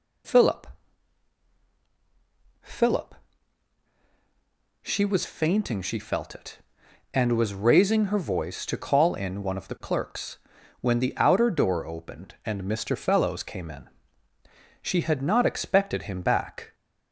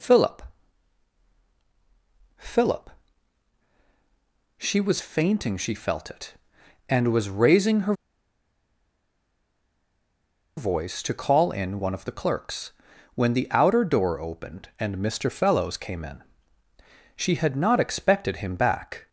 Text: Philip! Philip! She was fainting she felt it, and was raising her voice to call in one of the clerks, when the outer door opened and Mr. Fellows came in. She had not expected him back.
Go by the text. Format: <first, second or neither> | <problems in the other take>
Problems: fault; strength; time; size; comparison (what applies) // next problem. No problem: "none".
first | pauses between "her" and "voice"; strong; at 7.9 s; 2.6 s long